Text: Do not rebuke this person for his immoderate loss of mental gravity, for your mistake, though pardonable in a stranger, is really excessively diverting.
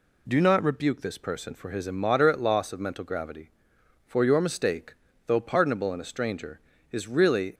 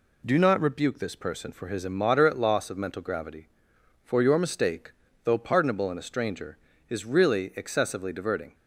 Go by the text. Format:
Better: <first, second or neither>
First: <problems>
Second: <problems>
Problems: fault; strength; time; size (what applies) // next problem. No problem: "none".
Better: second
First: stops before "excessively diverting"; at 7.5 s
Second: none